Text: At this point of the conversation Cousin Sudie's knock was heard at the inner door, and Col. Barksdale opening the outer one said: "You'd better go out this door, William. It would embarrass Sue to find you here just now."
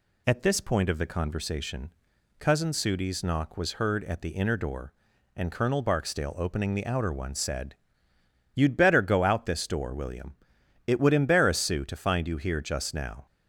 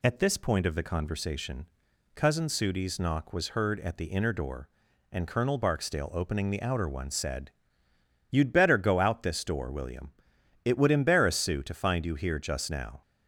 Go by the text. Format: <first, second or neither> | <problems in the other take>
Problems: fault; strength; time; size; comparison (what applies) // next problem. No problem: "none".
neither | pauses between "conversation" and "Cousin"; noticeable; the same in both